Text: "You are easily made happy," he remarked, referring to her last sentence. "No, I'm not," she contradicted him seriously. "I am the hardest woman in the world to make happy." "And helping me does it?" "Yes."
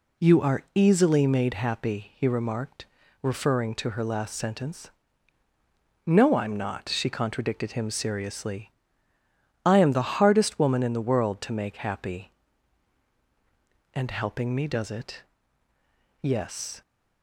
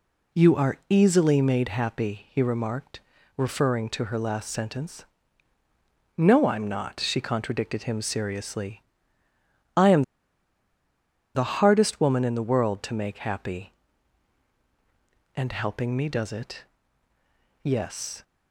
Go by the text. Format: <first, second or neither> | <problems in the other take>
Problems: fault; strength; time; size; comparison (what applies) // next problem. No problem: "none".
first | pauses between "am" and "the"; strong; at 10.0 s; 1.3 s long